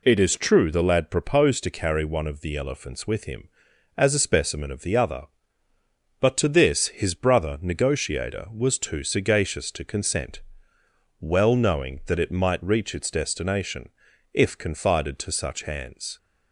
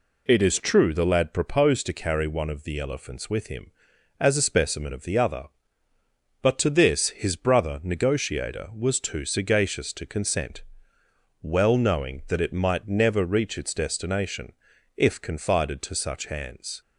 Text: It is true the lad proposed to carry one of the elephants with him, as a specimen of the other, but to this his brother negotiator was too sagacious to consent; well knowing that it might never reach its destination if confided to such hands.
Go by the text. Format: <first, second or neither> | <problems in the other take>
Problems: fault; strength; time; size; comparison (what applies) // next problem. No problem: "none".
second | skips "never"; at 12.6 s // pauses between "destination" and "if"; at 13.8 s; 0.44 s long; also in the second